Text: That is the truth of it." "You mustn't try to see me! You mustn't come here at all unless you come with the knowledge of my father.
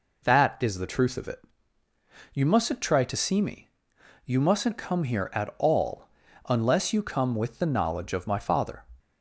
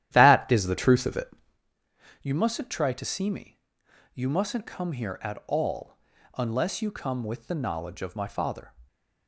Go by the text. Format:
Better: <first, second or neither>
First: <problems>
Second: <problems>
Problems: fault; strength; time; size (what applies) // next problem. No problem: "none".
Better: first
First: pauses between "all" and "unless"; at 6.0 s; 0.40 s long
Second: starts louder than the rest; strong; until 1.6 s; 12 dB // pauses between "all" and "unless"; at 5.9 s; 0.40 s long